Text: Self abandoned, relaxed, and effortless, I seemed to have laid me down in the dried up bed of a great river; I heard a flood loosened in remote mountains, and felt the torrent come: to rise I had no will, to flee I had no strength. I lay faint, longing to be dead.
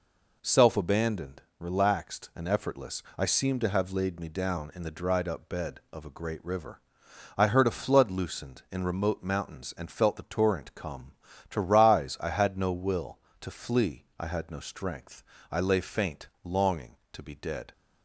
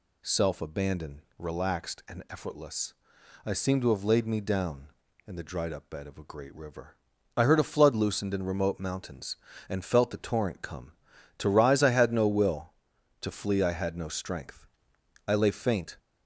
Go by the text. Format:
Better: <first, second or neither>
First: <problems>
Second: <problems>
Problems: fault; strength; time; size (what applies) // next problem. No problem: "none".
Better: first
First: none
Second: stops before "longing to be dead"; at 15.9 s